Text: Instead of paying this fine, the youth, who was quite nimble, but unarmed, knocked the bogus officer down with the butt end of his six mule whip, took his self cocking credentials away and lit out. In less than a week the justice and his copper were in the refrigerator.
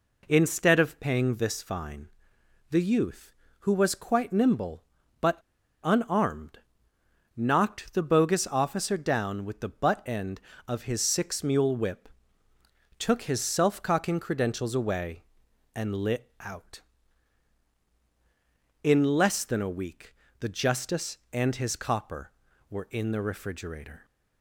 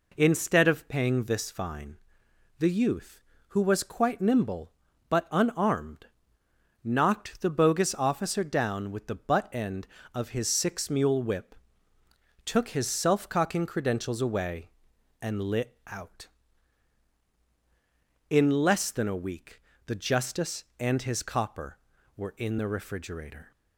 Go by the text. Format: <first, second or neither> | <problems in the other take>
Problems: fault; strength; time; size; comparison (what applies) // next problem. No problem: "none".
second | pauses between "but" and "unarmed"; at 5.3 s; 0.45 s long // pauses between "week" and "the"; slight; at 20.1 s; 0.24 s long; slight in the second